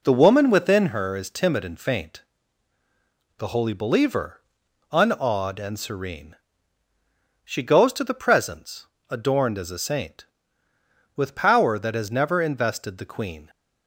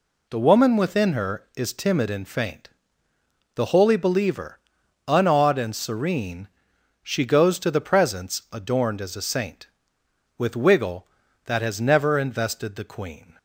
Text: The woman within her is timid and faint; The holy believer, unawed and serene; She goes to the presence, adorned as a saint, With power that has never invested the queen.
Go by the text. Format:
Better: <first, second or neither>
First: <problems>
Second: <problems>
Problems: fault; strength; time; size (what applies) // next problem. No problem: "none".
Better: first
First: none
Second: says "wiggle" for "power"; at 10.5 s